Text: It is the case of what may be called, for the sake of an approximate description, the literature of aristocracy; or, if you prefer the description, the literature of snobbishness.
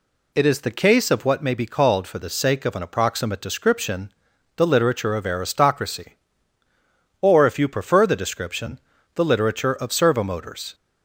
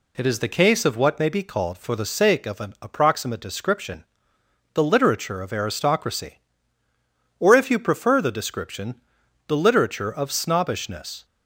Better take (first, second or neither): second